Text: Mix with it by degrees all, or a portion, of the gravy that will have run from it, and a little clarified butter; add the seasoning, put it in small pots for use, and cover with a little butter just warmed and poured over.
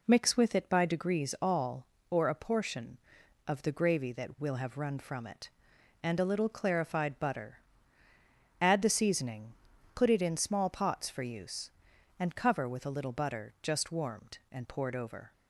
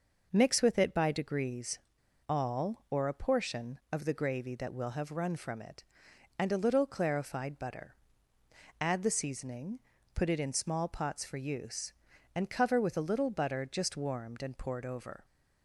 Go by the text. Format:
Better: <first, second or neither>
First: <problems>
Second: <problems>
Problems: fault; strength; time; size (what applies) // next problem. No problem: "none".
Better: first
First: none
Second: pauses between "degrees" and "all"; noticeable; at 1.7 s; 0.49 s long